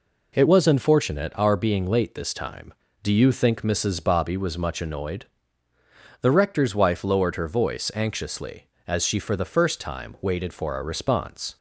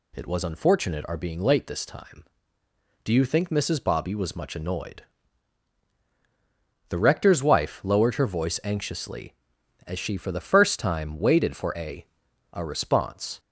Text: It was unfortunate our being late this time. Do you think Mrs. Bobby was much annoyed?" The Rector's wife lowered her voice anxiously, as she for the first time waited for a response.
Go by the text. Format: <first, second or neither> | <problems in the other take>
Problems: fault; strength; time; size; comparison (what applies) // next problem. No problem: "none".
first | says "a" twice; at 12.5 s